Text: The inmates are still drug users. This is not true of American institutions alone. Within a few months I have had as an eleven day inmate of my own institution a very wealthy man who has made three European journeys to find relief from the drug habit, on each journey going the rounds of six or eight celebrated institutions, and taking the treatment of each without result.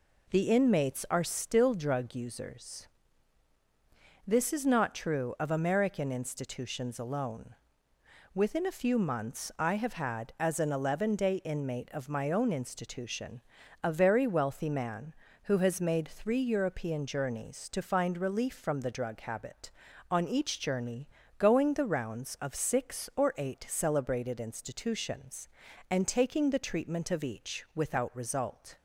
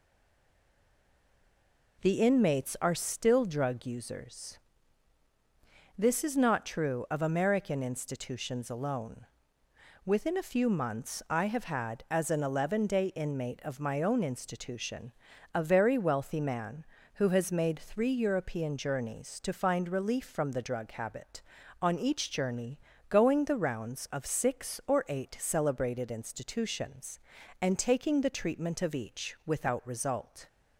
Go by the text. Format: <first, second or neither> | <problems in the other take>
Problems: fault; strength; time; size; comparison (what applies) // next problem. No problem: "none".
first | stays silent before the first word; noticeable; until 1.9 s; 1.9 s long // pauses between "institution" and "a"; at 15.1 s; 0.42 s long; also in the first // pauses between "journey" and "going"; slight; at 22.7 s; 0.30 s long; slight in the first